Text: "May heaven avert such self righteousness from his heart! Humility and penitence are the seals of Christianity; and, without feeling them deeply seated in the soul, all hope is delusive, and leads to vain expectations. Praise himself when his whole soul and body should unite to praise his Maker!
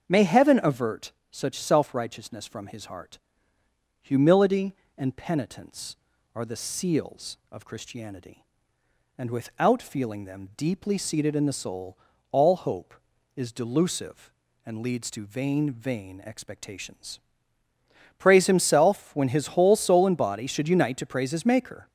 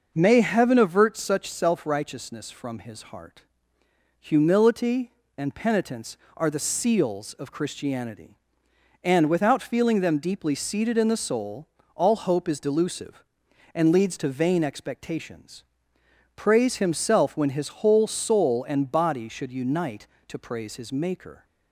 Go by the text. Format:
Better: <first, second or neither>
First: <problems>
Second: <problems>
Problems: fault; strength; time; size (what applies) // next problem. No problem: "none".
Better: second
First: starts louder than the rest; until 1.1 s; 7 dB // pauses between "avert" and "such"; slight; at 1.1 s; 0.18 s long // says "vain" twice; at 15.6 s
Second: none